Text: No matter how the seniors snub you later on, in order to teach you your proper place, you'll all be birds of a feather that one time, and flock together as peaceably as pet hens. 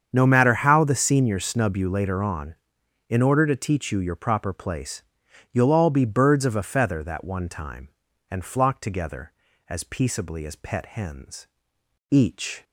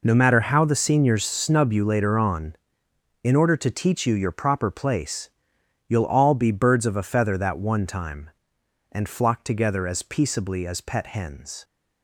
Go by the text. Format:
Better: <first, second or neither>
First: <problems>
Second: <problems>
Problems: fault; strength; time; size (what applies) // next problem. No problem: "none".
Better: second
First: starts louder than the rest; strong; until 1.1 s; 7.5 dB // goes on to say "Each"; from 12.0 s on; 0.54 s long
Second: none